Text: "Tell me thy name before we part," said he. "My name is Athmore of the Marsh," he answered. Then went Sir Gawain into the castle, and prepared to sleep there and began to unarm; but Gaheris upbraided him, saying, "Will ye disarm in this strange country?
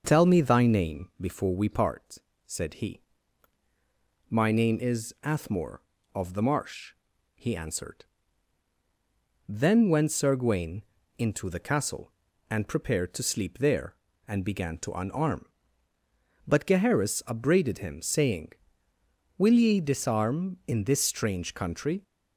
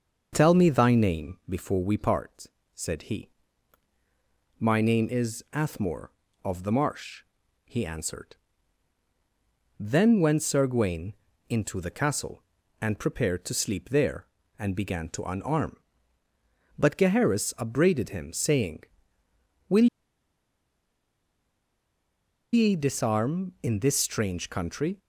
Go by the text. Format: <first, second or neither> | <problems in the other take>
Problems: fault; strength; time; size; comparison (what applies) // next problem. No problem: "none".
first | starts louder than the rest; until 1.3 s; 6.5 dB; also in the first // pauses between "Gawain" and "into"; slight; at 11.1 s; 0.36 s long; slight in the first // pauses between "Will" and "ye"; strong; at 19.8 s; 2.6 s long